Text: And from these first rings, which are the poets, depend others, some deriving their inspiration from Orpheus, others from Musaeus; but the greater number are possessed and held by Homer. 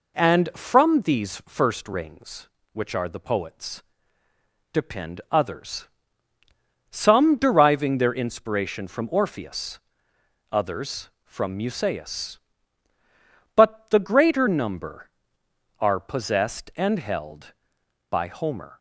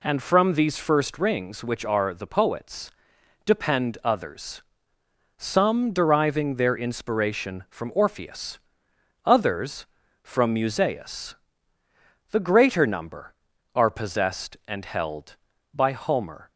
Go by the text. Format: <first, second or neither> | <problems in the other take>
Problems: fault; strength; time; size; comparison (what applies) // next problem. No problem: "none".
first | skips "but"; at 11.8 s